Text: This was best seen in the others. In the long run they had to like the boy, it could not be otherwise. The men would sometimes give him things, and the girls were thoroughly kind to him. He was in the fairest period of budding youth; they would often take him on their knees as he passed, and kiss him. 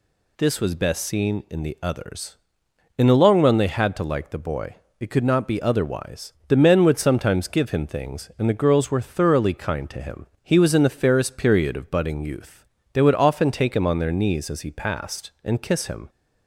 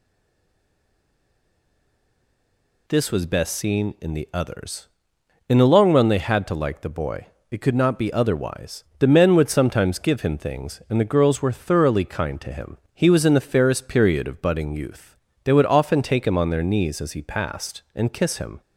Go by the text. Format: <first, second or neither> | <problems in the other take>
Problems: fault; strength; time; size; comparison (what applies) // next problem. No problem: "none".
first | stays silent before the first word; strong; until 2.8 s; 2.8 s long